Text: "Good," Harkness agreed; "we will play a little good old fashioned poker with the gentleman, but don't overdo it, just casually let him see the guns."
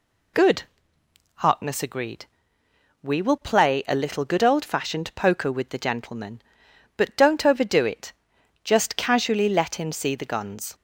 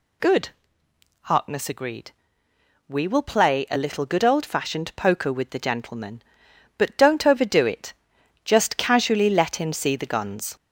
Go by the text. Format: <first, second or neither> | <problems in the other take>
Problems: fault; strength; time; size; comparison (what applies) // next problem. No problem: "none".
first | gets louder; slight; throughout; 3 dB